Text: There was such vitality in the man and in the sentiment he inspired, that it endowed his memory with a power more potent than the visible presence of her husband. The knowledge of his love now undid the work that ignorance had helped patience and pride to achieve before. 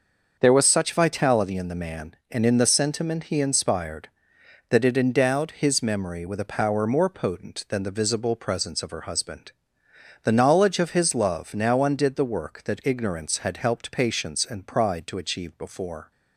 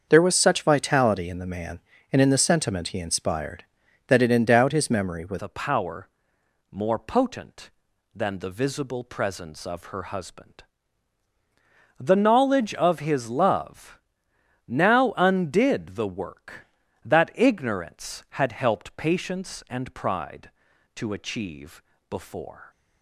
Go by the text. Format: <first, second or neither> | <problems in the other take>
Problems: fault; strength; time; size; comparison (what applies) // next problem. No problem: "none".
first | starts louder than the rest; until 1.0 s; 7 dB; also in the first // changes voice at "a"; from 5.3 s on; 17.3 s long // pauses between "power" and "more"; noticeable; at 6.0 s; 0.64 s long // pauses between "love" and "now"; noticeable; at 13.9 s; 0.66 s long // pauses between "achieve" and "before"; slight; at 21.8 s; 0.26 s long